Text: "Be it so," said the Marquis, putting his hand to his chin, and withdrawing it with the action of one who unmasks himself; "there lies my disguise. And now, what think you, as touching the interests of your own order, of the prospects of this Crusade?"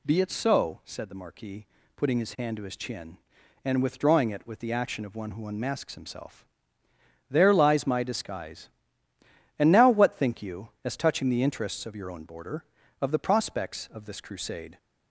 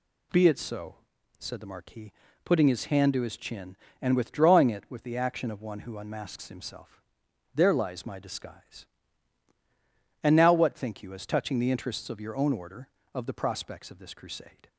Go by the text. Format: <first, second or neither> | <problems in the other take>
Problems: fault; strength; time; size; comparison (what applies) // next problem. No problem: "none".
second | says "border" for "order"; at 12.2 s